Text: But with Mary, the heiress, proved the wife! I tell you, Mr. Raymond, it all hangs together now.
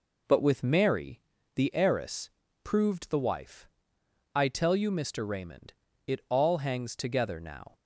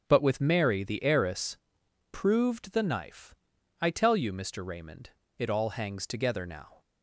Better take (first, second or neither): first